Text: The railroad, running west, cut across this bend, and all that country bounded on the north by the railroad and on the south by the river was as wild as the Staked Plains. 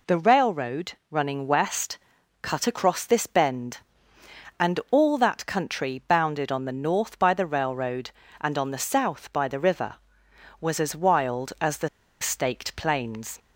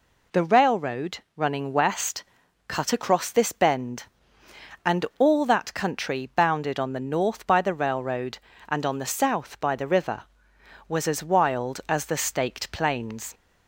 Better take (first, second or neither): second